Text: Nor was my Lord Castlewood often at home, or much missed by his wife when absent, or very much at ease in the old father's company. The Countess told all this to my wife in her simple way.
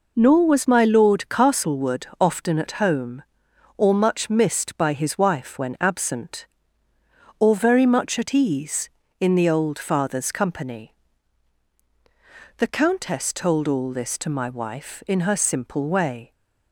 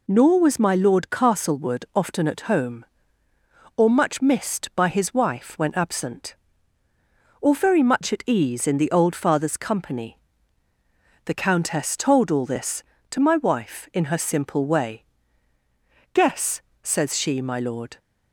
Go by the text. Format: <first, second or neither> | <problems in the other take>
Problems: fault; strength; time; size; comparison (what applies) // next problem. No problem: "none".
first | goes on to say "Guess says she my lord"; strong; from 16.1 s on; 1.8 s long